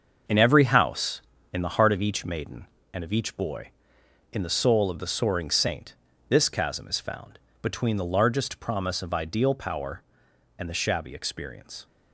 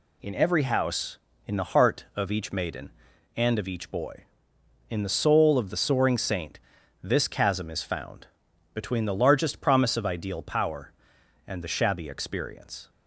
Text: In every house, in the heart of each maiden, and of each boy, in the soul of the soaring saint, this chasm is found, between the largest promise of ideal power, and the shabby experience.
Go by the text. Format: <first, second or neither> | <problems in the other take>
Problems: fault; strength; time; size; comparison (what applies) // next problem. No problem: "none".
second | gets quieter; strong; throughout; 8.5 dB